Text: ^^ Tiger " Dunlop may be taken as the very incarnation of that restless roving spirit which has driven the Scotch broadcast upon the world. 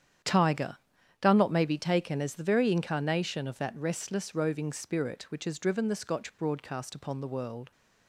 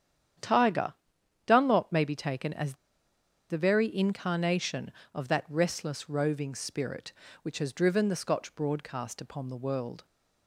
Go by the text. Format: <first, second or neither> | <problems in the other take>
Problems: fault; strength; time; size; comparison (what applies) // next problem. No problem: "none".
first | starts louder than the rest; strong; until 1.6 s; 8 dB; strong in the first // pauses between "as" and "the"; noticeable; at 2.7 s; 0.76 s long